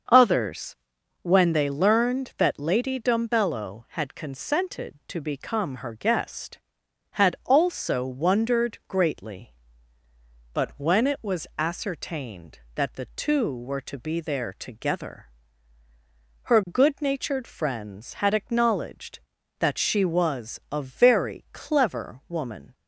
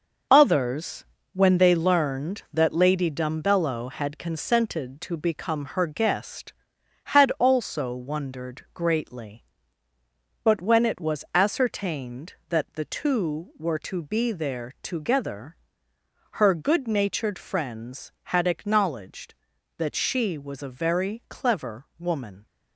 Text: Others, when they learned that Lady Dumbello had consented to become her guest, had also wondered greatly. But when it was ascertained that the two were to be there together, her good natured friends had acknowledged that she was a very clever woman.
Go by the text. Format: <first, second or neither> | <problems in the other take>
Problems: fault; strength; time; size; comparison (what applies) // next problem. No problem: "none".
first | gets quieter; strong; throughout; 7.5 dB // starts louder than the rest; noticeable; until 1.6 s; 6 dB; also in the first